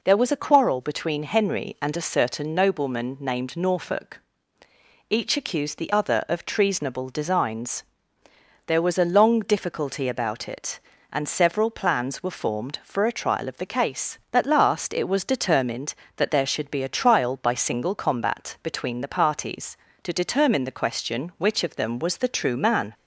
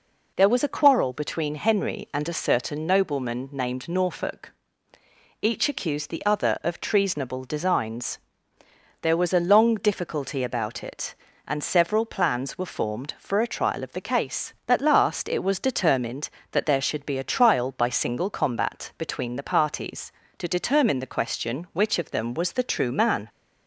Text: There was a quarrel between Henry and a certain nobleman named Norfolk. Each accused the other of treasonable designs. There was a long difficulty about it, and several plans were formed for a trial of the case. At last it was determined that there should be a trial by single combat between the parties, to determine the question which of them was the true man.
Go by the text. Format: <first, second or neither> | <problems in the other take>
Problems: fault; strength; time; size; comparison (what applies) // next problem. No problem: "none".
neither | none